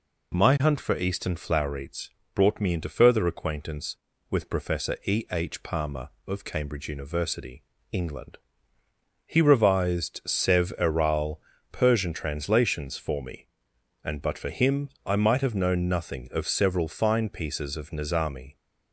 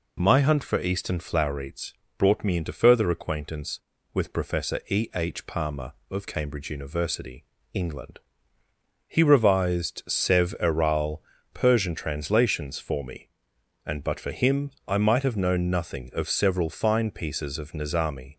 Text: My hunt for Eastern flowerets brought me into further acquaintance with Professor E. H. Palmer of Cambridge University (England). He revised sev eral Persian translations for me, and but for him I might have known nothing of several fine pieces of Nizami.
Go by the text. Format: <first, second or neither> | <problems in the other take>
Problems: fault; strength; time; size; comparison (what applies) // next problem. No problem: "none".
neither | pauses between "flowerets" and "brought"; slight; the same in both // pauses between "eral" and "Persian"; slight; the same in both // pauses between "him" and "I"; slight; the same in both